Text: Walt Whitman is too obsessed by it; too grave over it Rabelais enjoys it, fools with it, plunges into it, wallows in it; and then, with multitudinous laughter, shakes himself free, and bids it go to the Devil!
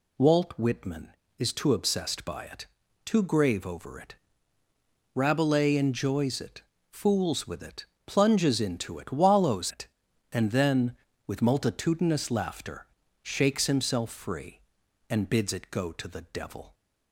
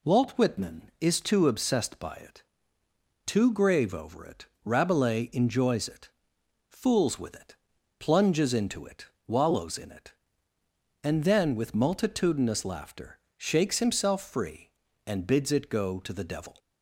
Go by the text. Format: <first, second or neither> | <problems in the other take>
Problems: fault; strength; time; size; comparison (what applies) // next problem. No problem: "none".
second | pauses between "it" and "Rabelais"; at 4.1 s; 1.0 s long; slight in the second // skips "in"; at 9.7 s